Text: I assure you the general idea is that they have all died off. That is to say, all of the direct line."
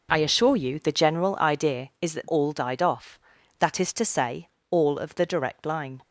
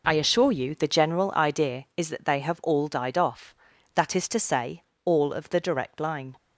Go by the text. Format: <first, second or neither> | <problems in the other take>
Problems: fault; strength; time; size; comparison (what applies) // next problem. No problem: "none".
second | skips "they have"; at 2.2 s